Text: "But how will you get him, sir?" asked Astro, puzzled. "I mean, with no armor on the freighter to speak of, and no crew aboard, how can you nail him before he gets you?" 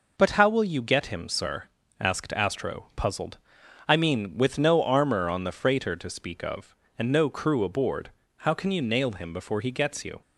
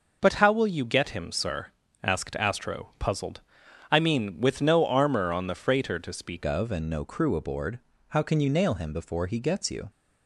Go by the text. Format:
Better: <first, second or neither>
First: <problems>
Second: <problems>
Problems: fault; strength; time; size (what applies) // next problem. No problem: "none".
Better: first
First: none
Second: changes voice at "of"; from 6.4 s on; 3.4 s long